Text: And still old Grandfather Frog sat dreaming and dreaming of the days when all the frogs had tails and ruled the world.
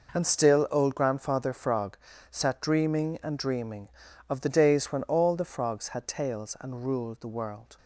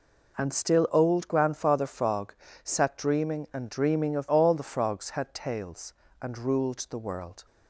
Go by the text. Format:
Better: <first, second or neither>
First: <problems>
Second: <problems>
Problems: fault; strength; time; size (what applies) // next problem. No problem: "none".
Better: first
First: pauses between "Frog" and "sat"; slight; at 1.9 s; 0.36 s long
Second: pauses between "Frog" and "sat"; slight; at 2.3 s; 0.30 s long // skips "the days when"; at 4.2 s